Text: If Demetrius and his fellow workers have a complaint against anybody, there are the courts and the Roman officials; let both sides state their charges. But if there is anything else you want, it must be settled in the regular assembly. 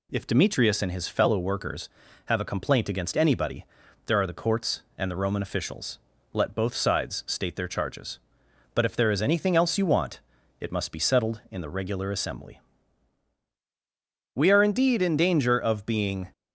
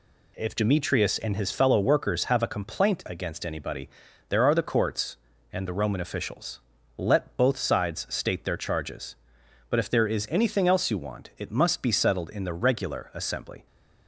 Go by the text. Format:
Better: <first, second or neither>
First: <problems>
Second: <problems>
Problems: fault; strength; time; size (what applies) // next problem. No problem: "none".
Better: second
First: goes on to say "We are indeed in danger of being"; strong; from 14.3 s on; 1.9 s long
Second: none